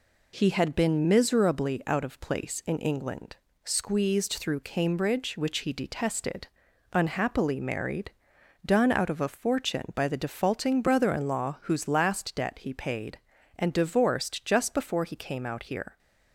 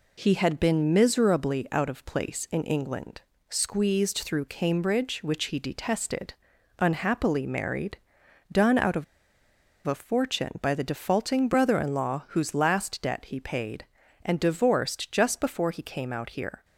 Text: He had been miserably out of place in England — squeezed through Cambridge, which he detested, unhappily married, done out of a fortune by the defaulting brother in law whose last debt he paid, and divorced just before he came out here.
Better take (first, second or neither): first